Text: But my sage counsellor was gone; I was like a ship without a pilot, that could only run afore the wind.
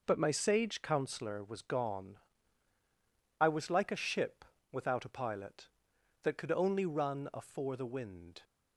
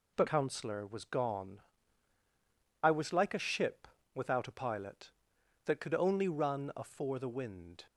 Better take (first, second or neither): first